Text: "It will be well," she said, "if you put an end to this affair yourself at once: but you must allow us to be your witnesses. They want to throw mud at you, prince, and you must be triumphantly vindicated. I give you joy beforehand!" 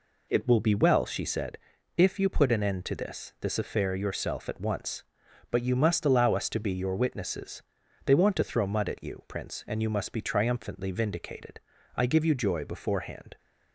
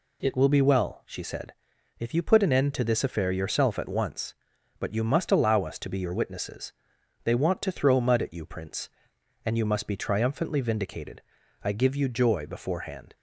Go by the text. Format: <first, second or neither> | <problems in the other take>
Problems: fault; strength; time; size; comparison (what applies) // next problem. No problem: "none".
second | says "this" twice; at 3.4 s